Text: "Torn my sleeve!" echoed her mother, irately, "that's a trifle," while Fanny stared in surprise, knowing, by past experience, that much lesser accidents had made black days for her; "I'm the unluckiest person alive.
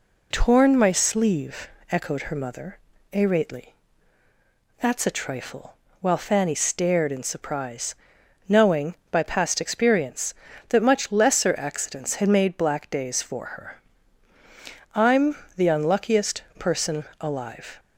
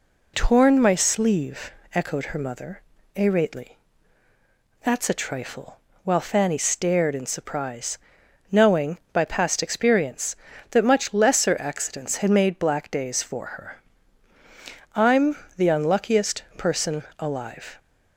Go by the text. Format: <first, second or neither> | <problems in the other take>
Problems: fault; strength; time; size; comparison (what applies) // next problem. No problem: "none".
neither | pauses between "I'm" and "the"; slight; the same in both // pauses between "person" and "alive"; slight; the same in both